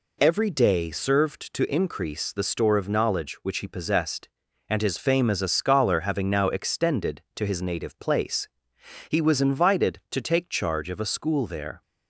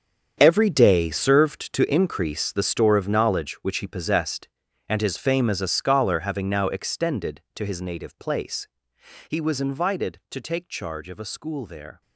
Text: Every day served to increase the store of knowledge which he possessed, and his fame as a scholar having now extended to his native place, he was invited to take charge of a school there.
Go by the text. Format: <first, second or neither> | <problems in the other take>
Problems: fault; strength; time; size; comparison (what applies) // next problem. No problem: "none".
first | gets quieter; strong; throughout; 13.5 dB